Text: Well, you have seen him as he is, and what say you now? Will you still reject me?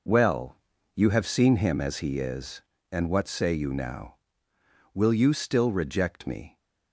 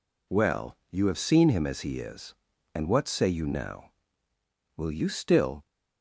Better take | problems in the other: first | stops before "reject me"; at 5.6 s

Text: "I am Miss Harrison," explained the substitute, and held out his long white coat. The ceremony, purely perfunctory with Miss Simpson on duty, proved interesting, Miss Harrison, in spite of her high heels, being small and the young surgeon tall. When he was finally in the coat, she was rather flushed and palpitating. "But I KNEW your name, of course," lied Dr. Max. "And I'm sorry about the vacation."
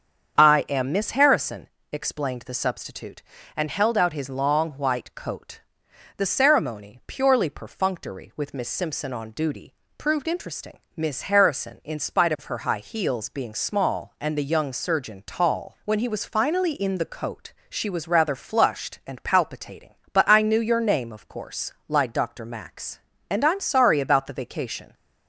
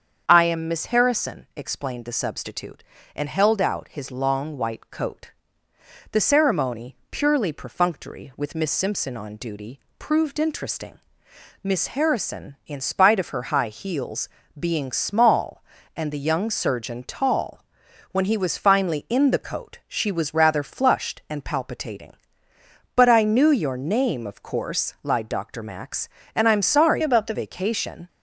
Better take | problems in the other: first | starts louder than the rest; strong; until 1.2 s; 7.5 dB; strong in the first // changes voice from "about" to "the"; from 27.0 to 27.3 s; 0.3 s long

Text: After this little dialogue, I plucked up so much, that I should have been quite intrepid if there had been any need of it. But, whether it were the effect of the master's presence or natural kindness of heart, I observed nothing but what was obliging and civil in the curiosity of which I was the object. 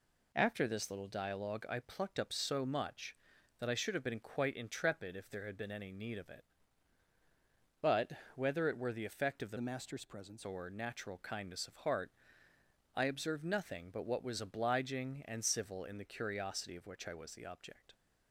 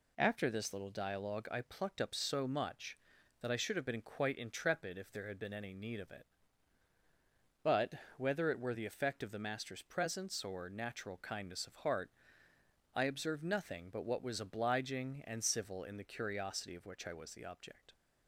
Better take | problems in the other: second | changes voice from "master's" to "presence"; from 9.5 to 10.4 s; 0.9 s long

